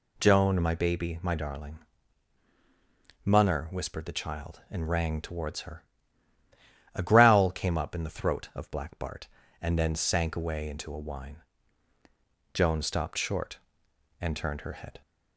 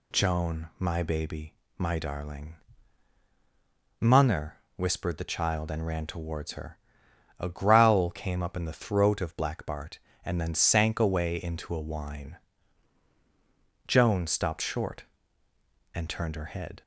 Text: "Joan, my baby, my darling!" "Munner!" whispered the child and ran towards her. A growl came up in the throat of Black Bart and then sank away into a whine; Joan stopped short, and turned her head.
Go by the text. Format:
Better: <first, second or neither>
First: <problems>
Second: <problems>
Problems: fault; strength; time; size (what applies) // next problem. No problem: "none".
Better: second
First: says "rang" for "ran"; at 4.8 s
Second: none